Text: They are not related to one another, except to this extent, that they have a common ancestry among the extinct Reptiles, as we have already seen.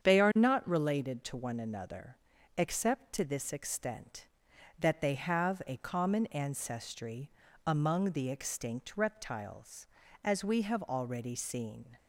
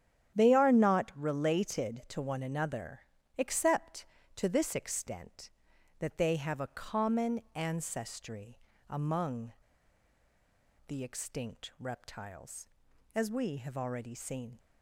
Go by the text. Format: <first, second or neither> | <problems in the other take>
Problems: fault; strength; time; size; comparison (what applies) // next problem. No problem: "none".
first | starts louder than the rest; strong; until 1.3 s; 10 dB; strong in the first // pauses between "ancestry" and "among"; slight; at 8.5 s; 0.32 s long; slight in the first // pauses between "among" and "the"; strong; at 9.5 s; 1.3 s long